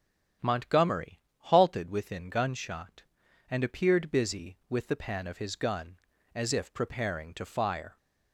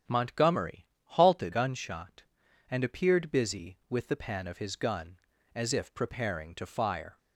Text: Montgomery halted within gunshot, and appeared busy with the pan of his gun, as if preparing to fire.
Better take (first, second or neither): first